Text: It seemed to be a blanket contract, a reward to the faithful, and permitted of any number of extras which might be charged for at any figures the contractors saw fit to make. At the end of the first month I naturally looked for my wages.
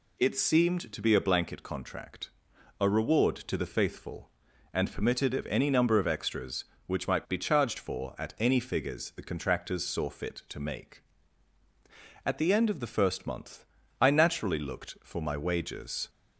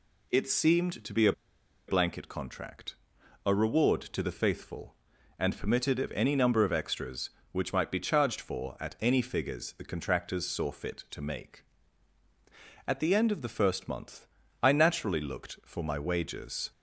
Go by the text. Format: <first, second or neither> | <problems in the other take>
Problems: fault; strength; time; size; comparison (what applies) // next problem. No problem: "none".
first | pauses between "a" and "blanket"; noticeable; at 1.3 s; 0.56 s long // pauses between "month" and "I"; slight; at 14.2 s; 0.34 s long; slight in the first